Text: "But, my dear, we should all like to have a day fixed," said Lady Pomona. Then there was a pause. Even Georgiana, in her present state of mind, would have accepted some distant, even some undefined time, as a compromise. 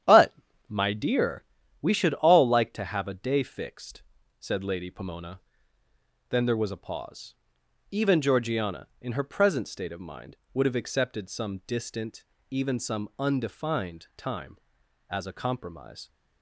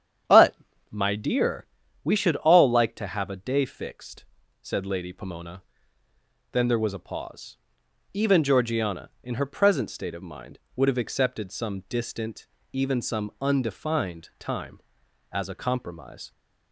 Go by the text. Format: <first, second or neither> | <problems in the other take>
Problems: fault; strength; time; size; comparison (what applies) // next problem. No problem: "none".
second | gets quieter; throughout; 6.5 dB // starts louder than the rest; strong; until 1.3 s; 10 dB; strong in the second